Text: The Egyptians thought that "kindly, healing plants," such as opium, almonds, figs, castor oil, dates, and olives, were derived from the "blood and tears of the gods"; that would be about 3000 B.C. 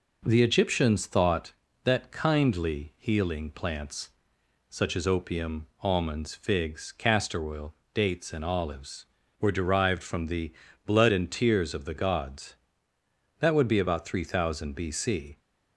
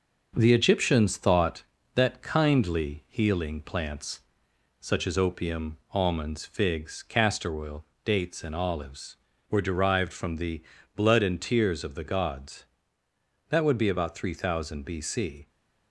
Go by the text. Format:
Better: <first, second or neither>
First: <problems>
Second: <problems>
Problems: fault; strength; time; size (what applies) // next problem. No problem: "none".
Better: first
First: pauses between "the" and "blood"; slight; at 10.5 s; 0.32 s long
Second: gets quieter; throughout; 3.5 dB // pauses between "the" and "blood"; slight; at 10.6 s; 0.32 s long